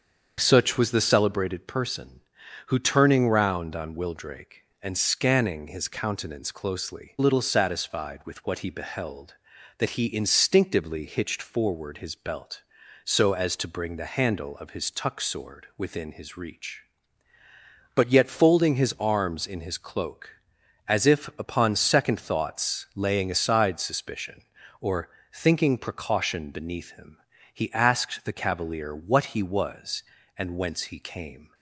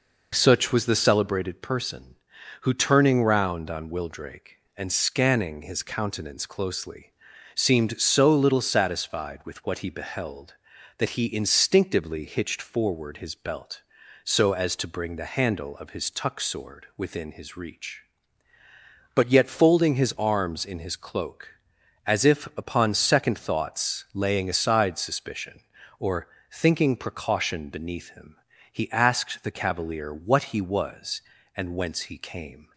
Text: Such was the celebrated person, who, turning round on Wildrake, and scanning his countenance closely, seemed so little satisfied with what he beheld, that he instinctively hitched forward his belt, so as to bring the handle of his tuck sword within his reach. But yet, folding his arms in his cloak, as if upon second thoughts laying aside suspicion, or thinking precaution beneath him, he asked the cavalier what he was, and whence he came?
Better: second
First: starts louder than the rest; until 1.3 s; 7 dB // skips "seemed so"; at 7.1 s // pauses between "or" and "thinking"; slight; at 25.0 s; 0.24 s long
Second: pauses between "or" and "thinking"; slight; at 26.2 s; 0.24 s long

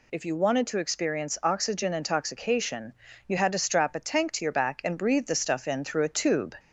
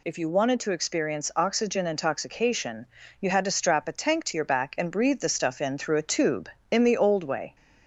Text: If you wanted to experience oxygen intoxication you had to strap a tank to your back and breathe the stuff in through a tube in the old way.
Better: second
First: pauses between "intoxication" and "you"; slight; at 2.9 s; 0.34 s long // stops before "in the old way"; at 6.5 s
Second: pauses between "intoxication" and "you"; slight; at 2.8 s; 0.34 s long

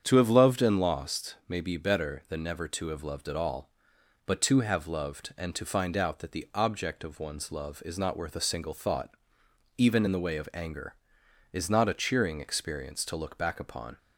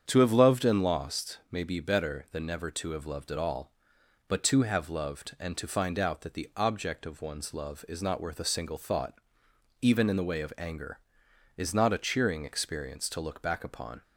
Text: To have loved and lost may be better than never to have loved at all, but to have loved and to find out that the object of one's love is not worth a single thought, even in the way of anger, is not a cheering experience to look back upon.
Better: neither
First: starts louder than the rest; strong; until 1.0 s; 8 dB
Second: starts louder than the rest; strong; until 1.0 s; 8 dB

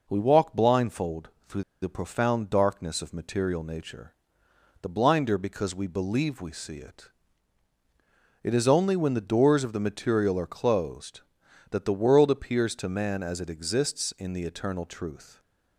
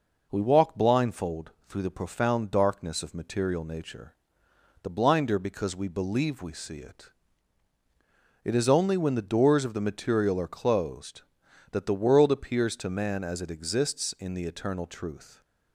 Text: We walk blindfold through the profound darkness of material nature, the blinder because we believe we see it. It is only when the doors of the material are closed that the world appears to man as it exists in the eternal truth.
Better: second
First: pauses between "blindfold" and "through"; slight; at 1.2 s; 0.20 s long // pauses between "through" and "the"; slight; at 1.6 s; 0.19 s long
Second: pauses between "blindfold" and "through"; slight; at 1.5 s; 0.18 s long

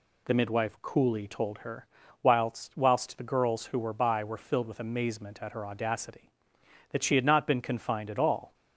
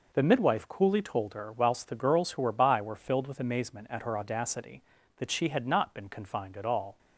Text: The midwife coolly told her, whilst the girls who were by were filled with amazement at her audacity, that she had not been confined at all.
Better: second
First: says "whilst" twice; at 2.7 s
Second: none

